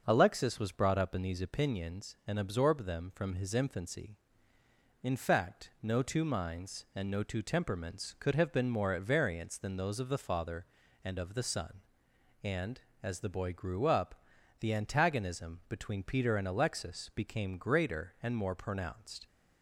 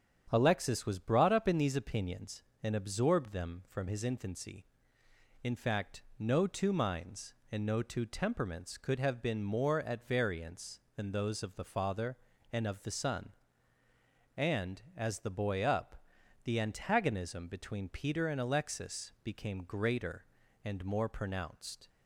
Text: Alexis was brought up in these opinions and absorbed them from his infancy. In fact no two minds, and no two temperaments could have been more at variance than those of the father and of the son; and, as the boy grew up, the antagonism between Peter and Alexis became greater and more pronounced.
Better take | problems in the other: first | starts louder than the rest; strong; until 1.3 s; 8.5 dB; noticeable in the first // pauses between "fact" and "no"; slight; at 6.0 s; 0.16 s long // skips "grew"; at 15.6 s

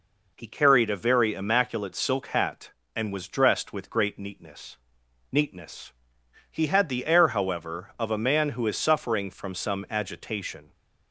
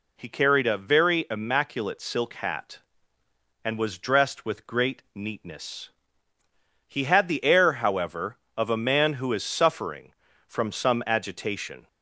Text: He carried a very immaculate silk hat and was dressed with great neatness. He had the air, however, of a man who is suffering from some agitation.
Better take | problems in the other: second | says "neatness" twice; at 5.3 s

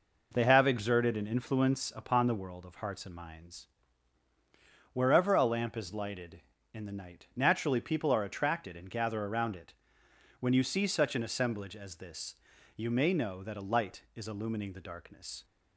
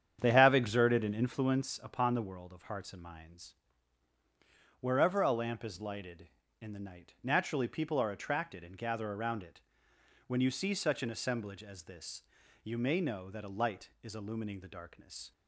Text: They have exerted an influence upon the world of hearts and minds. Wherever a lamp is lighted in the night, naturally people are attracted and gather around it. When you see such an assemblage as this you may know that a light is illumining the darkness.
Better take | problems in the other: first | starts louder than the rest; strong; until 1.6 s; 8.5 dB // pauses between "this" and "you"; at 12.2 s; 0.40 s long; also in the first

